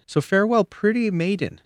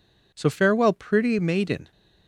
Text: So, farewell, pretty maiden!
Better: neither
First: none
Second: none

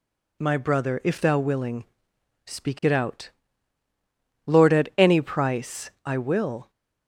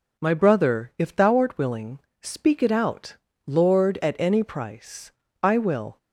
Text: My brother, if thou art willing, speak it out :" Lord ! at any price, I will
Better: second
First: skips "art"; at 1.3 s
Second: none

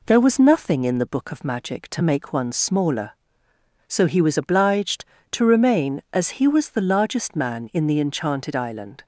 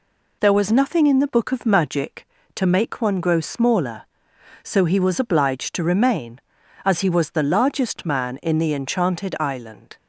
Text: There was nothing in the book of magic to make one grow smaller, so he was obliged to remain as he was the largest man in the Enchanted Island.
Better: second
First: skips "grow"; at 2.5 s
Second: none

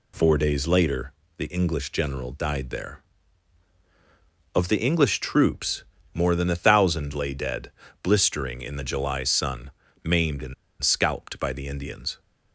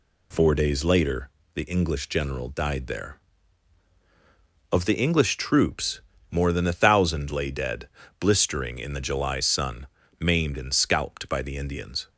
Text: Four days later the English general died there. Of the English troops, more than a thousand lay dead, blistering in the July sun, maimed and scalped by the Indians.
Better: second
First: pauses between "later" and "the"; slight; at 1.1 s; 0.28 s long // pauses between "and" and "scalped"; slight; at 10.5 s; 0.27 s long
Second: pauses between "later" and "the"; slight; at 1.2 s; 0.28 s long

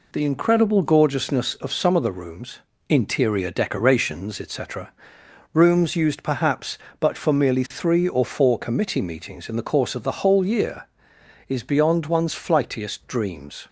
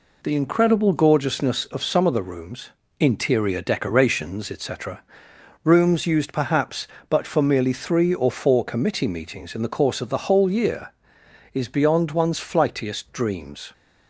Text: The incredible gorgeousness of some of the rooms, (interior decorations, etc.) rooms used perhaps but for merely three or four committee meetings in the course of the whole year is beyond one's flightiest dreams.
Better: neither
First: none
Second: none

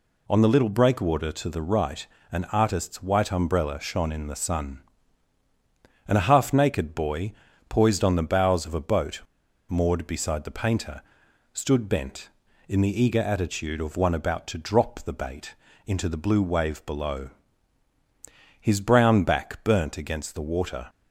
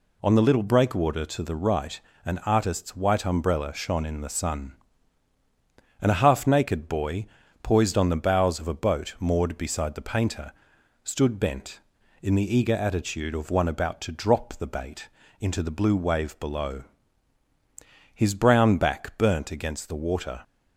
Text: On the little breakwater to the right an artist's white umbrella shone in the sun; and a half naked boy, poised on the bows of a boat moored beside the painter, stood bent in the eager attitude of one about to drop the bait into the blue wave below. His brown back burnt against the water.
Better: second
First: pauses between "right" and "an"; slight; at 2.0 s; 0.26 s long // pauses between "boat" and "moored"; noticeable; at 9.2 s; 0.49 s long // pauses between "bait" and "into"; slight; at 15.5 s; 0.30 s long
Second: pauses between "right" and "an"; slight; at 1.9 s; 0.26 s long // pauses between "bait" and "into"; slight; at 15.0 s; 0.30 s long

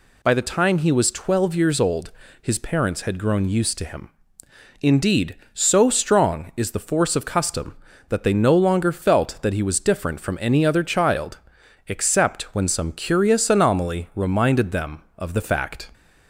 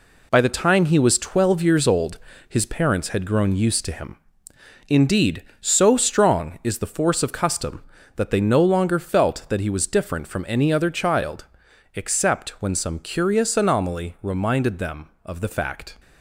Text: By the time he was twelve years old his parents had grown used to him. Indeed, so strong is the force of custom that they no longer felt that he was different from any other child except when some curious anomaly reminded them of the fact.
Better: first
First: pauses between "old" and "his"; slight; at 2.1 s; 0.30 s long // pauses between "child" and "except"; noticeable; at 11.3 s; 0.52 s long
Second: gets quieter; throughout; 7 dB // pauses between "old" and "his"; slight; at 2.1 s; 0.30 s long // pauses between "child" and "except"; noticeable; at 11.4 s; 0.52 s long

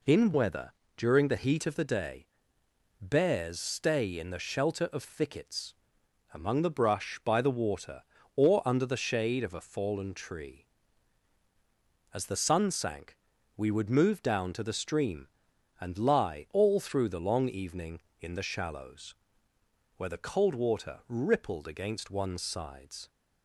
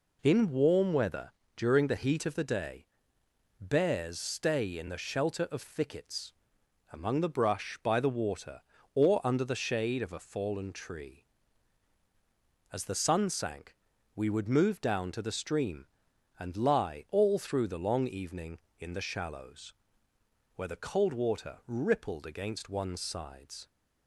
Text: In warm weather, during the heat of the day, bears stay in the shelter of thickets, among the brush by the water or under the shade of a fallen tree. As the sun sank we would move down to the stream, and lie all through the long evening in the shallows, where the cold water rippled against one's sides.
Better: second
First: skips "warm"; at 0.3 s // pauses between "sank" and "we"; at 13.1 s; 0.40 s long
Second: pauses between "sank" and "we"; at 13.7 s; 0.40 s long

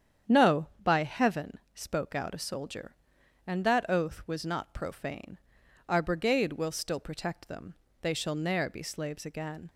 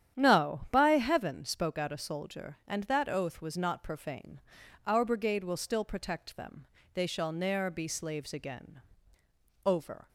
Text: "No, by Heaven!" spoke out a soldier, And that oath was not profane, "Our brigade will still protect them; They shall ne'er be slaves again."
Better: first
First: starts louder than the rest; strong; until 1.4 s; 8.5 dB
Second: starts louder than the rest; strong; until 1.2 s; 10 dB // goes on to say "Over"; slight; from 9.6 s on; 0.44 s long

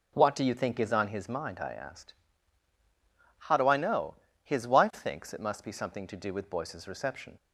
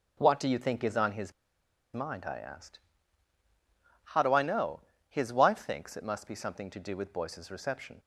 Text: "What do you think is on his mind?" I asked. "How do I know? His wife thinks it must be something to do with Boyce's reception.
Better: first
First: none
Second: pauses between "his" and "mind"; noticeable; at 1.3 s; 0.61 s long

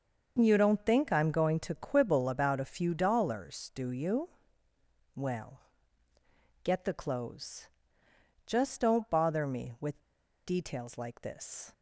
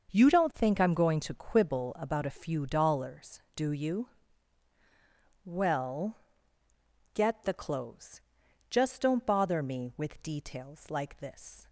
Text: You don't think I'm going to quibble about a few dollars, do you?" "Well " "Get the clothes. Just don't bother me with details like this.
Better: second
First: starts louder than the rest; until 1.4 s; 6.5 dB // pauses between "with" and "details"; noticeable; at 9.9 s; 0.47 s long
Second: starts louder than the rest; until 1.1 s; 6.5 dB

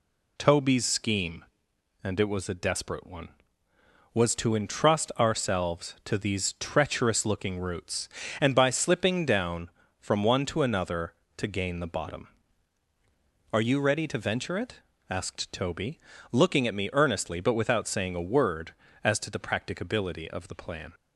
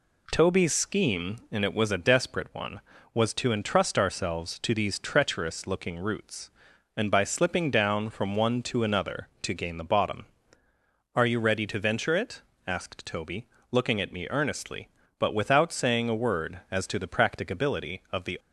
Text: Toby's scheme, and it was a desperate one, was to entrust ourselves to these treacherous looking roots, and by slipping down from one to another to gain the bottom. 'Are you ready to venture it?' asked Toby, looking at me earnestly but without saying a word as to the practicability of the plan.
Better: first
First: none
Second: stops before "plan"; at 18.3 s

